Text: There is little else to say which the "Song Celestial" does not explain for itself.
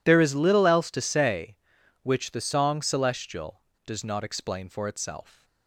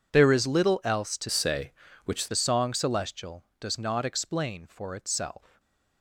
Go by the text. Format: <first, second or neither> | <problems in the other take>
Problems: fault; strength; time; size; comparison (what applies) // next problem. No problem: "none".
first | changes voice from "say" to "which"; from 1.2 to 2.2 s; 1.0 s long // stays silent after the last word; slight; from 5.3 s on; 0.7 s long